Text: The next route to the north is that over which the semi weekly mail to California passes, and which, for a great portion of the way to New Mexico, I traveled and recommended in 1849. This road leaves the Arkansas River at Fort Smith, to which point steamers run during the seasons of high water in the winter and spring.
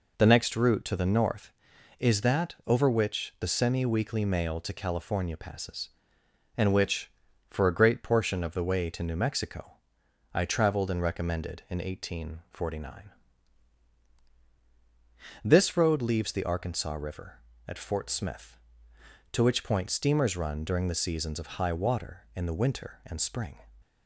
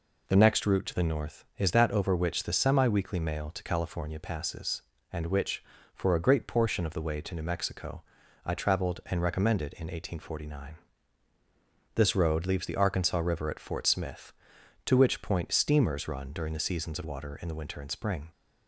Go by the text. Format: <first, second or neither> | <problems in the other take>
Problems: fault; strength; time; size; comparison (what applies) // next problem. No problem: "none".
first | skips "high"; at 17.0 s